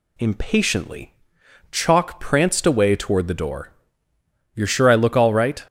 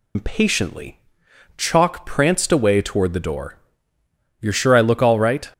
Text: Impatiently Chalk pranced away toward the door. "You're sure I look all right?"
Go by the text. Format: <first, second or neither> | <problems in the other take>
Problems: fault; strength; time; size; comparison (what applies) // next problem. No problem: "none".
first | loses the start of "Impatiently"; at 0.1 s; 130 ms // pauses between "Impatiently" and "Chalk"; noticeable; at 0.9 s; 0.56 s long; noticeable in the first